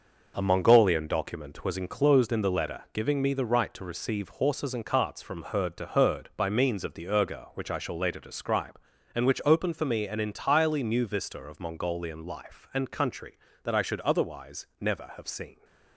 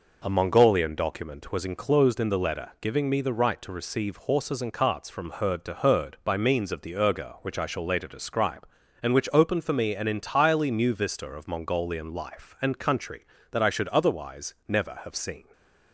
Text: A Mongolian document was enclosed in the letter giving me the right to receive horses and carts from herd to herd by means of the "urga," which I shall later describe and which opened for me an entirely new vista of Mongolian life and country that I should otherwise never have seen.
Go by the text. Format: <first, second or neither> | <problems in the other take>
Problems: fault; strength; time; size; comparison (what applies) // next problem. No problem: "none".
second | gets quieter; throughout; 6.5 dB